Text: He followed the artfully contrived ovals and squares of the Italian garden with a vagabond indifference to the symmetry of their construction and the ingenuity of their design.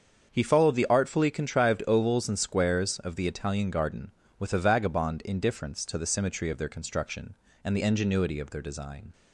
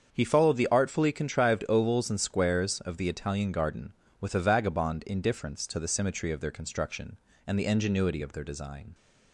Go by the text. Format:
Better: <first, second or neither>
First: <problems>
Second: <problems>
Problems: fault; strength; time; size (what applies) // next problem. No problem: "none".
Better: neither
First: starts louder than the rest; until 1.3 s; 7 dB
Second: starts louder than the rest; until 1.1 s; 7 dB